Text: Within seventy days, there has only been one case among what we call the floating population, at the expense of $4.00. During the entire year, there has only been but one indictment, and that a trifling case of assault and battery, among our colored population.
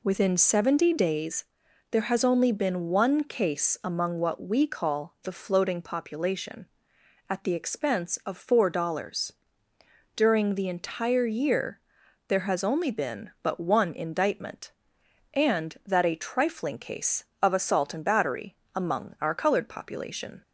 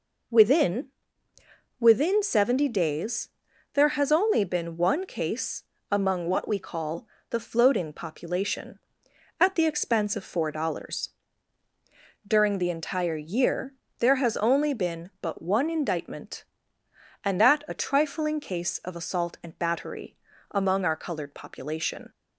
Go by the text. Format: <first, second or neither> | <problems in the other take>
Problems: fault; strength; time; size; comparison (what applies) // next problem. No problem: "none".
first | says "Within" twice; at 1.7 s // pauses between "case" and "among"; slight; at 5.6 s; 0.26 s long // pauses between "call" and "the"; slight; at 7.0 s; 0.22 s long